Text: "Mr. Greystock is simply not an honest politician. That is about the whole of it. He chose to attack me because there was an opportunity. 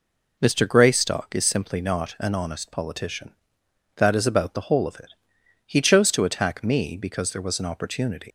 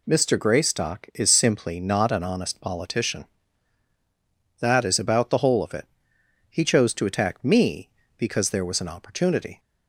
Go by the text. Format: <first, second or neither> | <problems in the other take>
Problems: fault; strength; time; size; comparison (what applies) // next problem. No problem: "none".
second | leaves "opportunity" unfinished; at 8.2 s; 130 ms